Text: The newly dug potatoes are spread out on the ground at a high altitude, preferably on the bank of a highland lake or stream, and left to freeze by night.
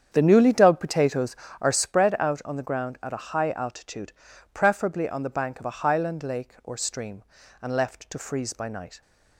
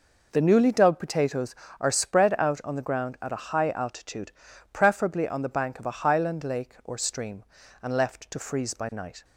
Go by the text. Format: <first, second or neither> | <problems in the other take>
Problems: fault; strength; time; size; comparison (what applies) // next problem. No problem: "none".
second | starts louder than the rest; strong; until 1.9 s; 8.5 dB